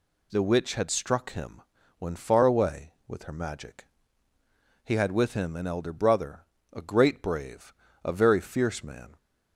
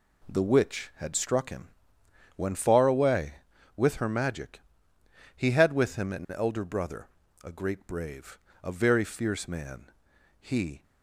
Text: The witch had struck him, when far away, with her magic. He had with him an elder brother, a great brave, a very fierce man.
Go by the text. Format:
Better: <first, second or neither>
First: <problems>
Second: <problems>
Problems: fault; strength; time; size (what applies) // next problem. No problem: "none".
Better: first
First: none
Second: goes on to say "He"; slight; from 10.3 s on; 0.44 s long